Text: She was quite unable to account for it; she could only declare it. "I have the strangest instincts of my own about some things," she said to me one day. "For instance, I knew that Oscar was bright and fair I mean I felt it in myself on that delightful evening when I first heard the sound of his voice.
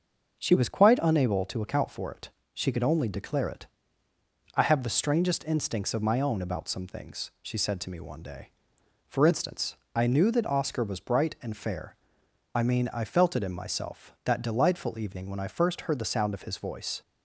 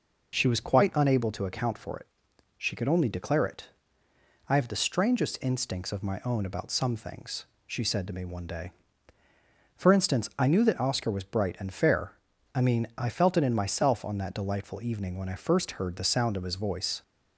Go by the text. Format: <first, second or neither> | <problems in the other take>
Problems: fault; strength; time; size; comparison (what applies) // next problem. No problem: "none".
second | starts louder than the rest; until 1.4 s; 6.5 dB // pauses between "fair" and "I"; noticeable; at 11.9 s; 0.58 s long; also in the second // skips "on"; at 14.1 s